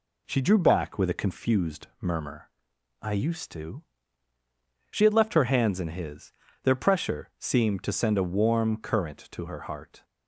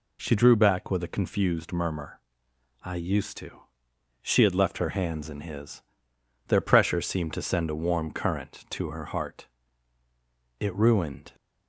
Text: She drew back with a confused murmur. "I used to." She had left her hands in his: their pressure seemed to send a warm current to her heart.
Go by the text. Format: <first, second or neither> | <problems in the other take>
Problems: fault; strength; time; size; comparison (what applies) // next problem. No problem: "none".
first | goes on to say "It ruined"; noticeable; from 10.5 s on; 0.76 s long